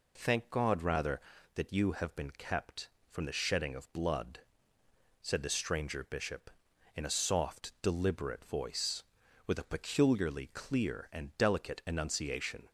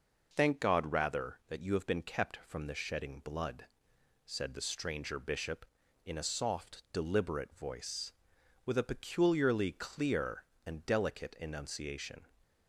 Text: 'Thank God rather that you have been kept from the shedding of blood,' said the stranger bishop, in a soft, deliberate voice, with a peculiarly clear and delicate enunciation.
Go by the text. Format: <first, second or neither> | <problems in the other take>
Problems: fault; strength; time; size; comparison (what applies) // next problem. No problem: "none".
first | skips "of"; at 3.1 s